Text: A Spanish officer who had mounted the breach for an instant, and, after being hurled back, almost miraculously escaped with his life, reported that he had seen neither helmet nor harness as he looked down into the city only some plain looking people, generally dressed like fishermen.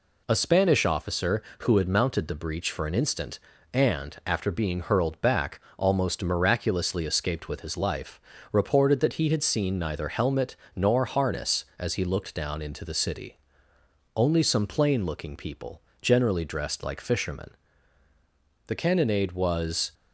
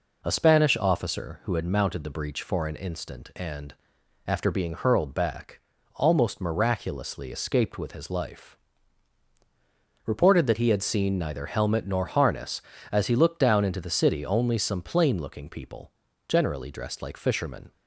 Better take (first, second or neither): second